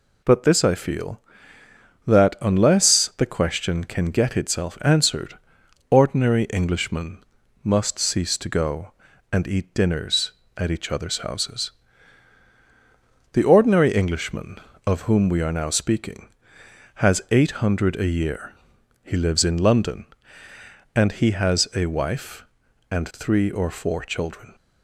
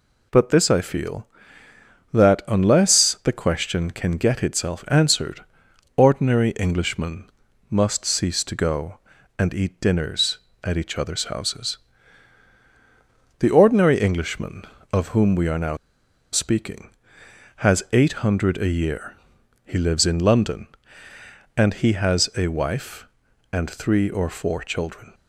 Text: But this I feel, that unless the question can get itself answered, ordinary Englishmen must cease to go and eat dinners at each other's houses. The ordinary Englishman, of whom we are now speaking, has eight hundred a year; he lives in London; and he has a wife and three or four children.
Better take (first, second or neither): first